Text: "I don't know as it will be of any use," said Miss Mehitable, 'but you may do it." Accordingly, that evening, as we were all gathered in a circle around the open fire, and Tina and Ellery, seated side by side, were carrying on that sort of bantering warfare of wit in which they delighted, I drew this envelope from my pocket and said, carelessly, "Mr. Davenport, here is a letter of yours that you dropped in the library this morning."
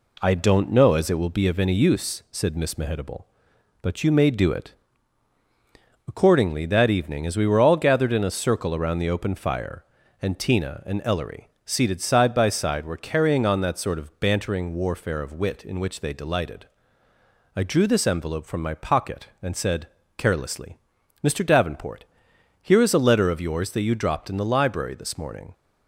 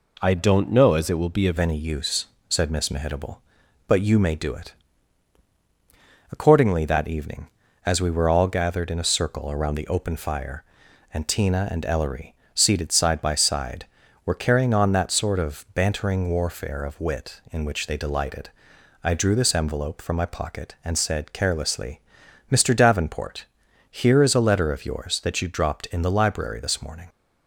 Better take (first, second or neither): first